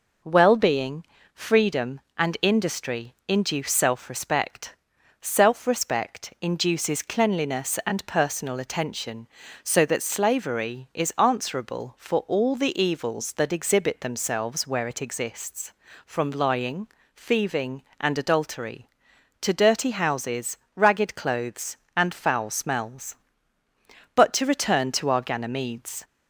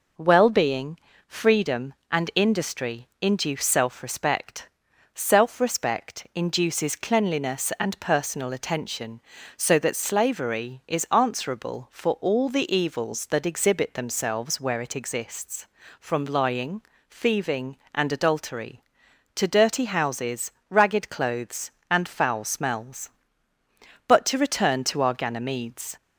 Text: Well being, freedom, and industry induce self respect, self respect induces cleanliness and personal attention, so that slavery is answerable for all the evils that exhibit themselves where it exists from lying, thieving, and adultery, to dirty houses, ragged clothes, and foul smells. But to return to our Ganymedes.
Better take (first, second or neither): neither